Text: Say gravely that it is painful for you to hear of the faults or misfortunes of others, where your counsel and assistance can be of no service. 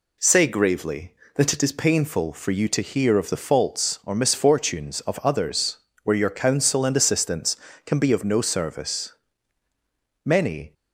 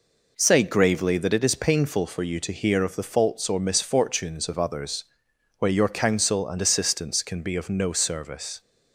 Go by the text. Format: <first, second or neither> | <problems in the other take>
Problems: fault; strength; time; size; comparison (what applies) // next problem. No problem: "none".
second | goes on to say "Many"; slight; from 10.2 s on; 0.48 s long